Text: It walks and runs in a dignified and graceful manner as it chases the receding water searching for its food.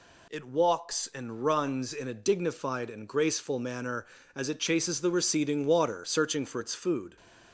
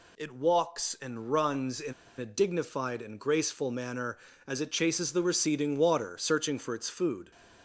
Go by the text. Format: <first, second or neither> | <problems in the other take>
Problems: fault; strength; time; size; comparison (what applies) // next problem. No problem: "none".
first | pauses between "in" and "a"; slight; at 1.9 s; 0.25 s long